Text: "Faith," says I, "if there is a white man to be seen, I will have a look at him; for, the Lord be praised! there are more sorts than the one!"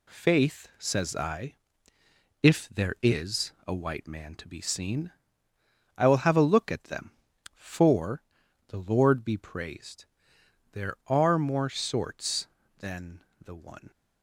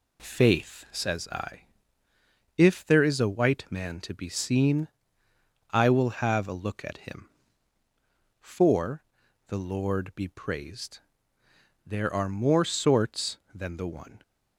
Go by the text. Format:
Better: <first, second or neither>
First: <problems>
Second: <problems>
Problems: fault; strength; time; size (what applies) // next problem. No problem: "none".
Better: second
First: says "them" for "him"; at 6.8 s // pauses between "than" and "the"; slight; at 13.2 s; 0.16 s long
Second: none